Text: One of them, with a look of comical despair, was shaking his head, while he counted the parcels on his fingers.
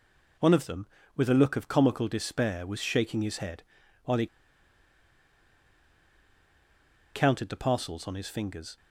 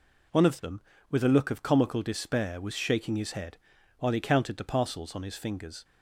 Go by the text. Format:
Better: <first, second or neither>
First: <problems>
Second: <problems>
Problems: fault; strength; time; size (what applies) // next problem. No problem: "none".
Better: second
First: pauses between "he" and "counted"; strong; at 4.2 s; 2.8 s long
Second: none